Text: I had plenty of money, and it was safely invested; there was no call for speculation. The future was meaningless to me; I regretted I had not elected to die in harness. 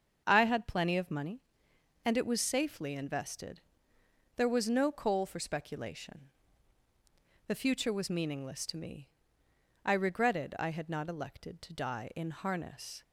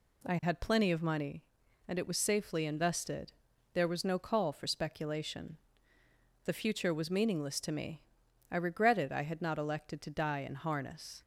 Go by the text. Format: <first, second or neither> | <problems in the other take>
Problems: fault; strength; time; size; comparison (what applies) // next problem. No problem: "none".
second | starts louder than the rest; until 1.2 s; 7 dB // says "coal" for "call"; at 4.8 s